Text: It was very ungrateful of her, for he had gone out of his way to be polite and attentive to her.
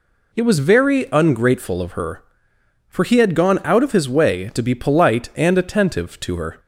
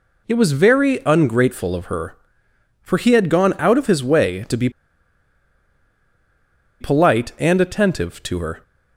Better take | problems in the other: first | pauses between "be" and "polite"; strong; at 4.7 s; 2.1 s long

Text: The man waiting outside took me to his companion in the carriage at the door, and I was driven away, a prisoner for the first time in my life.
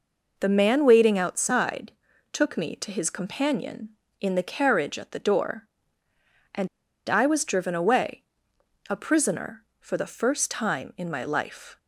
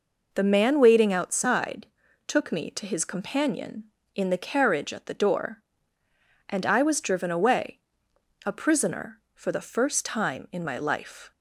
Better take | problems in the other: second | pauses between "outside" and "took"; at 1.9 s; 0.38 s long; also in the second // pauses between "and" and "I"; at 6.6 s; 0.41 s long

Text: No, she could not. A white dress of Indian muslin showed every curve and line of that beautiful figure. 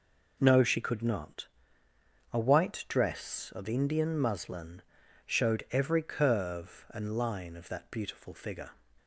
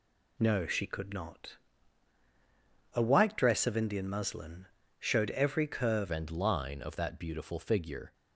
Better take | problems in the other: first | pauses between "muslin" and "showed"; slight; at 4.6 s; 0.32 s long; also in the first // changes voice at "and"; from 6.1 s on; 2.0 s long

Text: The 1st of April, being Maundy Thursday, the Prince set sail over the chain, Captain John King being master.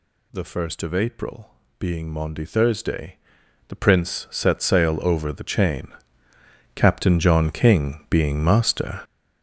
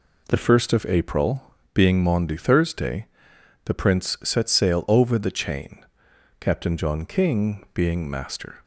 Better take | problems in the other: second | gets louder; strong; throughout; 10.5 dB

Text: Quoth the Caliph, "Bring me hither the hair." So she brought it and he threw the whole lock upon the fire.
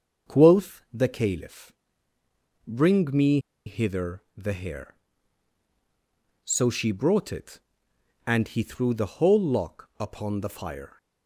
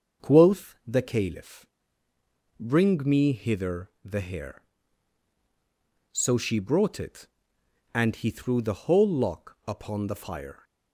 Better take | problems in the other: second | starts louder than the rest; until 1.3 s; 6.5 dB; also in the second // pauses between "me" and "hither"; slight; at 3.3 s; 0.27 s long

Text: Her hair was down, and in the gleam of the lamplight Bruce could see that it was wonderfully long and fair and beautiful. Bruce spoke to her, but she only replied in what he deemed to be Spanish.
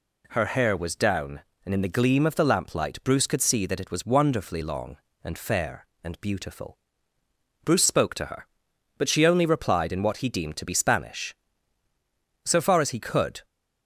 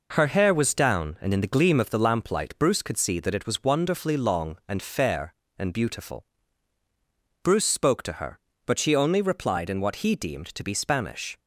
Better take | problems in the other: second | goes on to say "So far as he could"; noticeable; from 12.4 s on; 1.0 s long

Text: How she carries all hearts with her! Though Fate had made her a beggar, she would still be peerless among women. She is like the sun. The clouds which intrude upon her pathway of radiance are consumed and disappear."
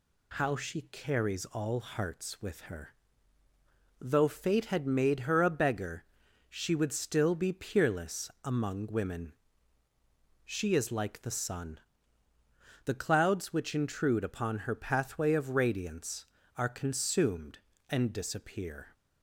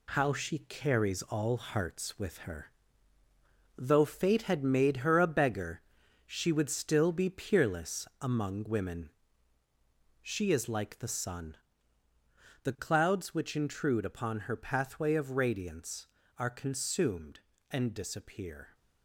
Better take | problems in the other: first | gets quieter; noticeable; throughout; 5.5 dB

